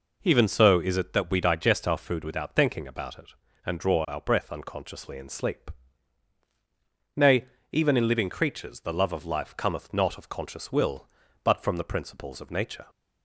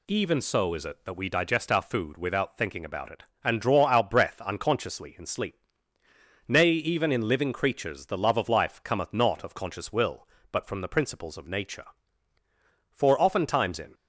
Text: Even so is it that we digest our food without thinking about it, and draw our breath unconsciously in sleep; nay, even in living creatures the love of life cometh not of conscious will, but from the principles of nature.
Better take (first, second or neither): first